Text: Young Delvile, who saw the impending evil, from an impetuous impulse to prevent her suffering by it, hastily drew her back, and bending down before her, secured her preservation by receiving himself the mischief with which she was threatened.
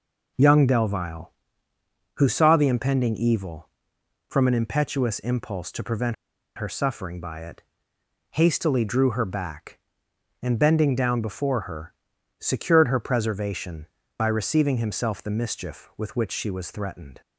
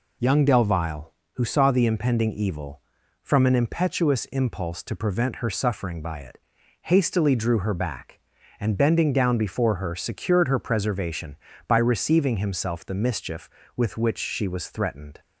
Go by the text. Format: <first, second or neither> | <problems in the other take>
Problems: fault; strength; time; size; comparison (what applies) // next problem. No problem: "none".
second | pauses between "prevent" and "her"; at 6.1 s; 0.41 s long